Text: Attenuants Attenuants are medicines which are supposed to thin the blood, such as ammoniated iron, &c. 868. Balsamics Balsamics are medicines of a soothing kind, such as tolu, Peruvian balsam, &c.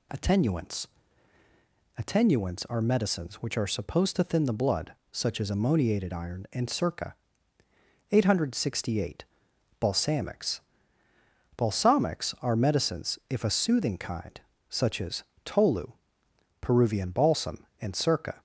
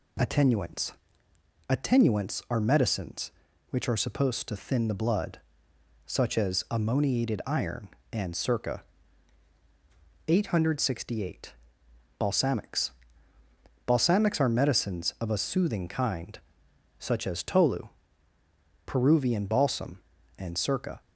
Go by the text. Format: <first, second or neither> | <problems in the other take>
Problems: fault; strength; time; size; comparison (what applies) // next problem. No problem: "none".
second | pauses between "Attenuants" and "Attenuants"; at 0.8 s; 1.1 s long; noticeable in the second // pauses between "Balsamics" and "Balsamics"; noticeable; at 10.6 s; 0.96 s long; noticeable in the second // says "if" for "of"; at 13.2 s // pauses between "as" and "tolu"; slight; at 15.2 s; 0.22 s long